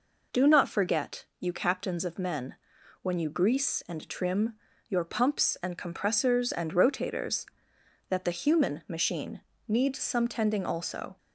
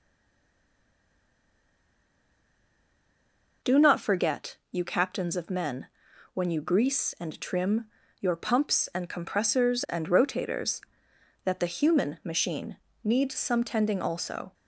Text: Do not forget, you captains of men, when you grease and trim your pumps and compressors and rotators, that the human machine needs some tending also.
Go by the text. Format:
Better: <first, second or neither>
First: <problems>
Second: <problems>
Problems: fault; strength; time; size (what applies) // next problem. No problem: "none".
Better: first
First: pauses between "trim" and "your"; slight; at 4.5 s; 0.34 s long // pauses between "machine" and "needs"; slight; at 9.4 s; 0.26 s long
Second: stays silent before the first word; strong; until 3.6 s; 3.6 s long // pauses between "trim" and "your"; slight; at 7.8 s; 0.34 s long // pauses between "machine" and "needs"; slight; at 12.7 s; 0.26 s long